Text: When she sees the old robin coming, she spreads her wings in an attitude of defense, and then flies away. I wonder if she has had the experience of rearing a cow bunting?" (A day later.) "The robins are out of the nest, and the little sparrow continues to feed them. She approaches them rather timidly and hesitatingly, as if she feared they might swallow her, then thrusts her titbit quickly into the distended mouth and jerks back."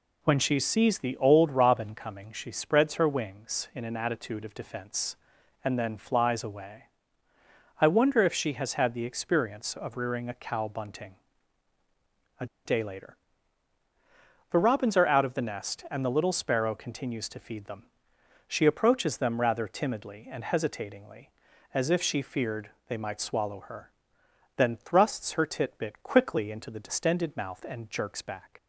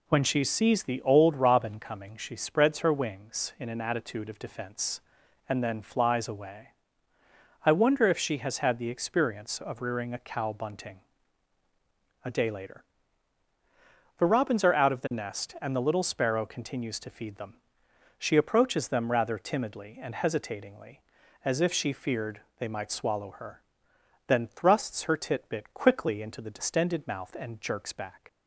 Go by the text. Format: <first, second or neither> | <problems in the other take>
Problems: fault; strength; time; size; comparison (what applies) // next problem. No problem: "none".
second | pauses between "A" and "day"; slight; at 12.4 s; 0.20 s long // pauses between "feared" and "they"; slight; at 22.7 s; 0.16 s long; slight in the second